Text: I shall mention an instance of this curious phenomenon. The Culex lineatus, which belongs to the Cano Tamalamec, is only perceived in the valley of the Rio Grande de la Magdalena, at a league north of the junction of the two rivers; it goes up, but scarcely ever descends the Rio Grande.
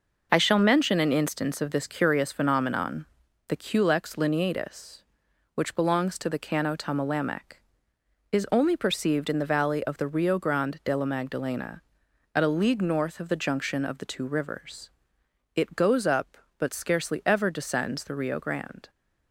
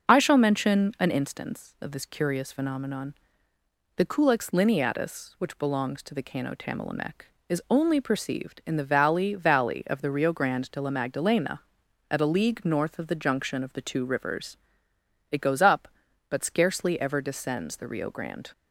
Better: first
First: none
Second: starts louder than the rest; until 1.1 s; 6.5 dB // says "valley" twice; at 9.3 s

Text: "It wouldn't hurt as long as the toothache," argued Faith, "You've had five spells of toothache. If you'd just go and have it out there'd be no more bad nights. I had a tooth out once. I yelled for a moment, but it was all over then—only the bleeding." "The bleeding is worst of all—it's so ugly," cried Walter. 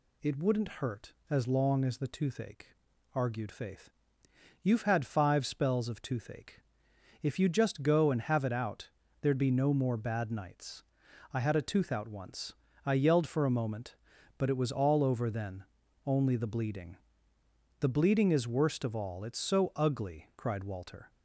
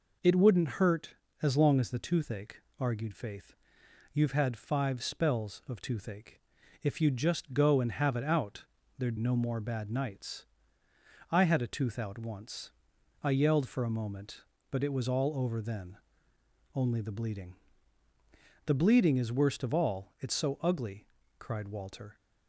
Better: first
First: pauses between "out" and "there'd"; slight; at 8.9 s; 0.32 s long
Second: pauses between "out" and "there'd"; slight; at 8.6 s; 0.32 s long // skips "be"; at 9.1 s

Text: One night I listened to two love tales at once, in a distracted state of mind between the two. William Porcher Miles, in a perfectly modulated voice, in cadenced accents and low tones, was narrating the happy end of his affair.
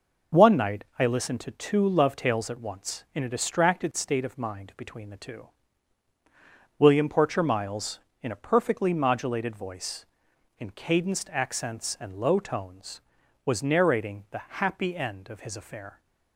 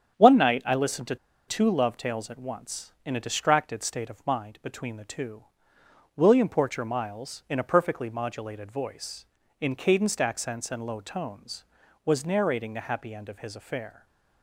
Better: first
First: none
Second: starts louder than the rest; strong; until 1.5 s; 8.5 dB // pauses between "to" and "two"; slight; at 1.1 s; 0.31 s long // stays silent after the last word; slight; from 13.9 s on; 0.5 s long

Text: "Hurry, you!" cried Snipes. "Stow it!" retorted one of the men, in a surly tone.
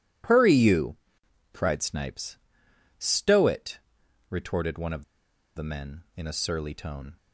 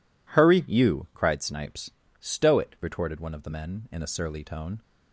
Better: second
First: pauses between "of" and "the"; noticeable; at 5.0 s; 0.52 s long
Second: none

